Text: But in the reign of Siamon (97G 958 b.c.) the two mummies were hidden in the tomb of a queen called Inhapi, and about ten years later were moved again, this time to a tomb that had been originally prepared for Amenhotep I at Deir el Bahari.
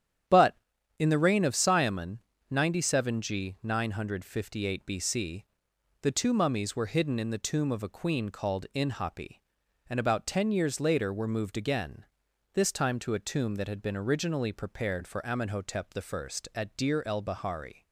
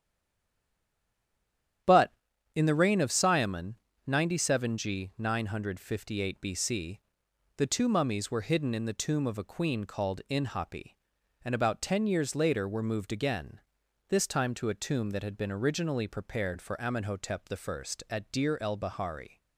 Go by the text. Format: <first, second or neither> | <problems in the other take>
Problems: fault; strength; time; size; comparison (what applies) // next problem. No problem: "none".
first | stays silent before the first word; noticeable; until 1.8 s; 1.8 s long // starts louder than the rest; strong; until 3.3 s; 9.5 dB; strong in the first